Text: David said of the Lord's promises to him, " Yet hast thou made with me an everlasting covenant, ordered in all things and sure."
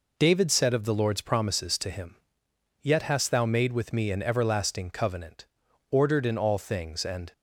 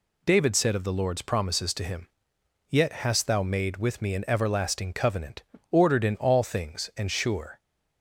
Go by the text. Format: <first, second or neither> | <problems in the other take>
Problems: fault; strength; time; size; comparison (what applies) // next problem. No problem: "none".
second | stops before "sure"; at 7.3 s